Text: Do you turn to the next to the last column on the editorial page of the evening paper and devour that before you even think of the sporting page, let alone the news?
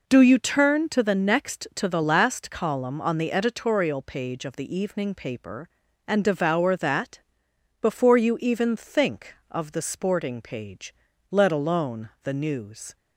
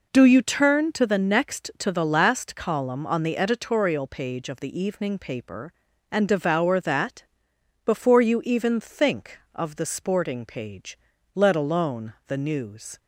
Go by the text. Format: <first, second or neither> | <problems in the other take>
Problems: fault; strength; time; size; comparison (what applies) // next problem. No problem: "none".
neither | pauses between "that" and "before"; noticeable; the same in both